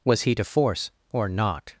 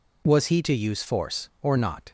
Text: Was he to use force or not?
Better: second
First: skips "use"; at 0.4 s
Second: none

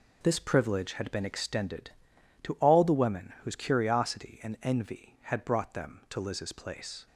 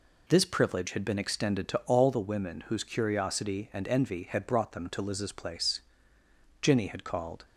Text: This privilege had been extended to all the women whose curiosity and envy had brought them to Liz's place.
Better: first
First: none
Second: goes on to say "Jinny had called"; noticeable; from 6.6 s on; 0.84 s long

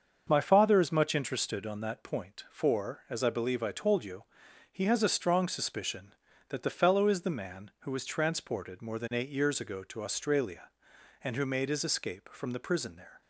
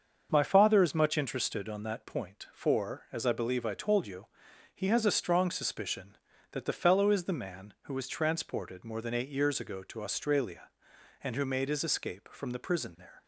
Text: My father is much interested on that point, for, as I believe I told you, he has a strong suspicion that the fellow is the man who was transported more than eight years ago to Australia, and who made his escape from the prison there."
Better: neither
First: starts louder than the rest; until 1.2 s; 6.5 dB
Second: starts louder than the rest; until 1.3 s; 6.5 dB

